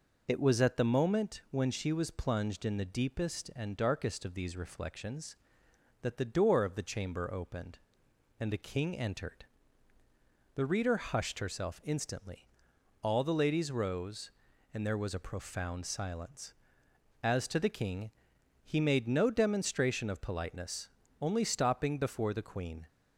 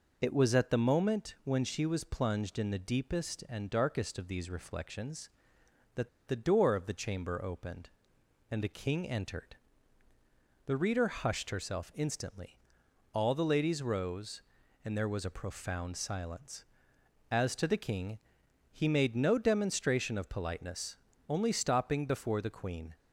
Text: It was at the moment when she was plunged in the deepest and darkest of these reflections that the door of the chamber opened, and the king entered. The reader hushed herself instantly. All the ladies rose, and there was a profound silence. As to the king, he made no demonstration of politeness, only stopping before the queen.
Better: first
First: none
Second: pauses between "that" and "the"; slight; at 6.0 s; 0.18 s long

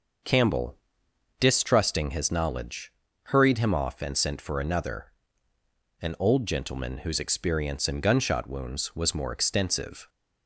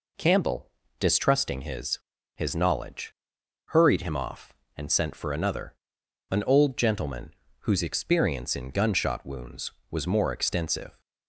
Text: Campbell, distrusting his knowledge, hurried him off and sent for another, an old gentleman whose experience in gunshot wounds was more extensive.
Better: first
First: none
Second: says "his" twice; at 2.3 s // pauses between "gentleman" and "whose"; slight; at 7.3 s; 0.28 s long

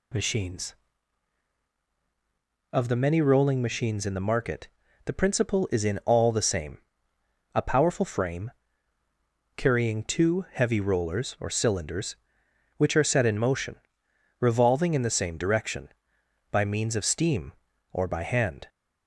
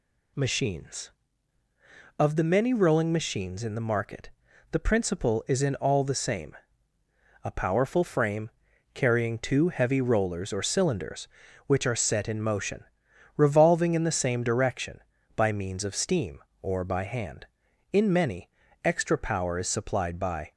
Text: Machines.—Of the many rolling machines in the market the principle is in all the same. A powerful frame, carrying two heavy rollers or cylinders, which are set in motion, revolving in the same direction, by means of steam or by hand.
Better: first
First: pauses between "market" and "the"; at 4.6 s; 0.38 s long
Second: pauses between "market" and "the"; at 4.2 s; 0.42 s long // goes on to say "In many extra power is supplied by"; strong; from 17.9 s on; 2.6 s long

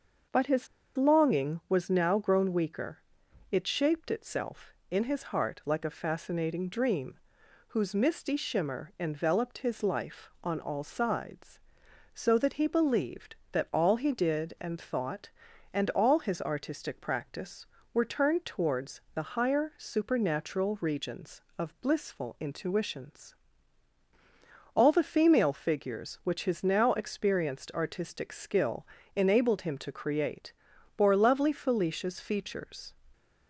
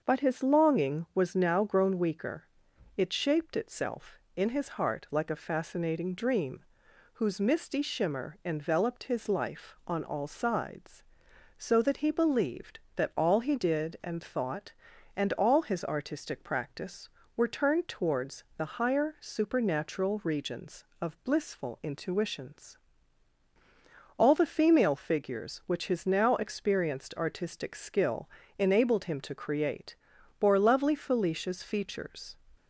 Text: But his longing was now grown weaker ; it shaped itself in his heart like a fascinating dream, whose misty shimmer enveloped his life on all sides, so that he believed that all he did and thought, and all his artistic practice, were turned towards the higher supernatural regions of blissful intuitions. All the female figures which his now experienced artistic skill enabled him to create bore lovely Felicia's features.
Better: second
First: starts louder than the rest; until 1.6 s; 6.5 dB // pauses between "his" and "longing"; slight; at 0.6 s; 0.29 s long // pauses between "skill" and "enabled"; slight; at 28.8 s; 0.28 s long // pauses between "create" and "bore"; at 30.5 s; 0.44 s long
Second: starts louder than the rest; until 1.0 s; 6.5 dB // pauses between "skill" and "enabled"; slight; at 28.2 s; 0.28 s long // pauses between "create" and "bore"; at 29.9 s; 0.44 s long

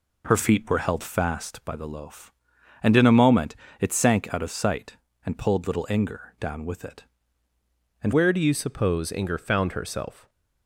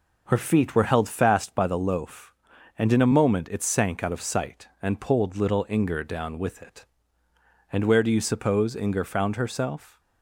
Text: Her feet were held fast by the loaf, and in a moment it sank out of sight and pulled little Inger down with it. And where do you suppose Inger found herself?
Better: second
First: pauses between "moment" and "it"; slight; at 3.5 s; 0.26 s long // changes voice at "where"; from 8.1 s on; 2.1 s long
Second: none

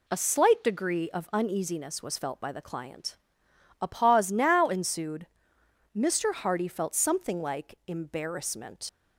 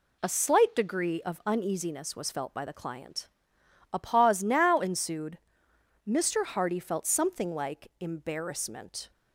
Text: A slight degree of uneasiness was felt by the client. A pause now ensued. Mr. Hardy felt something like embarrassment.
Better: second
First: leaves "embarrassment" unfinished; at 8.8 s; 85 ms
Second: none

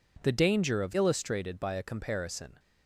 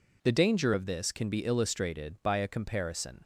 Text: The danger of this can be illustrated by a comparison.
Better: second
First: skips "this can be"; at 0.9 s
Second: none

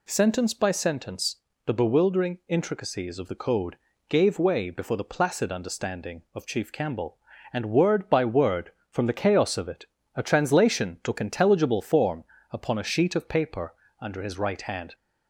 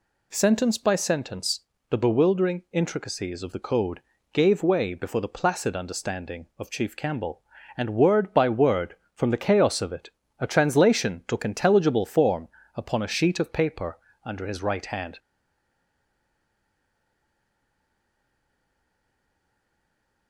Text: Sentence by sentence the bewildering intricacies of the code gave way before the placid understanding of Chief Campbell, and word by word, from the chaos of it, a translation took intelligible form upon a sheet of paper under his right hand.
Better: first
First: pauses between "sentence" and "the"; slight; at 1.3 s; 0.26 s long // pauses between "code" and "gave"; slight; at 3.7 s; 0.34 s long // pauses between "form" and "upon"; slight; at 12.2 s; 0.30 s long // pauses between "paper" and "under"; slight; at 13.7 s; 0.26 s long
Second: pauses between "sentence" and "the"; slight; at 1.6 s; 0.26 s long // pauses between "code" and "gave"; slight; at 3.9 s; 0.34 s long // pauses between "form" and "upon"; slight; at 12.4 s; 0.30 s long // pauses between "paper" and "under"; slight; at 13.9 s; 0.26 s long // stays silent after the last word; strong; from 15.1 s on; 5.1 s long

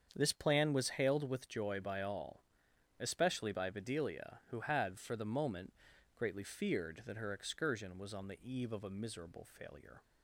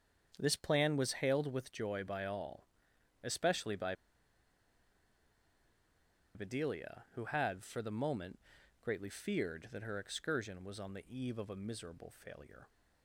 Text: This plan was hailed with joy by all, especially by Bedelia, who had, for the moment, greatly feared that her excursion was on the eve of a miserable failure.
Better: first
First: starts louder than the rest; strong; until 1.1 s; 7.5 dB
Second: starts louder than the rest; strong; until 1.3 s; 7.5 dB // pauses between "by" and "Bedelia"; strong; at 3.9 s; 2.3 s long

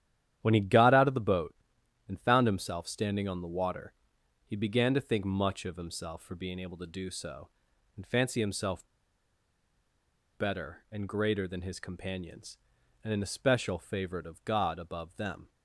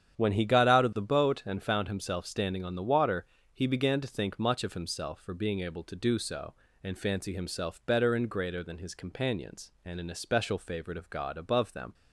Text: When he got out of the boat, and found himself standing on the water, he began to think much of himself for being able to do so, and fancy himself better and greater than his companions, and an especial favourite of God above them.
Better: second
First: starts louder than the rest; strong; until 1.4 s; 10.5 dB // pauses between "himself" and "better"; strong; at 8.8 s; 1.5 s long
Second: starts louder than the rest; strong; until 1.2 s; 9 dB

